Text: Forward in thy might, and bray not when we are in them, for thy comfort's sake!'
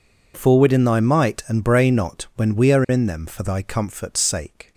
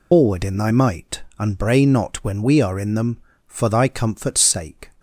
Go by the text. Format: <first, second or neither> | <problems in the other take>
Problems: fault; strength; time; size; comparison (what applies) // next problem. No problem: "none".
first | loses the start of "Forward"; at 0.1 s; 125 ms